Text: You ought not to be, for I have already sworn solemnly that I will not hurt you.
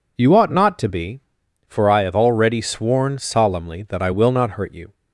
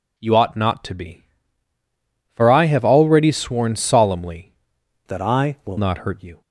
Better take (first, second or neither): first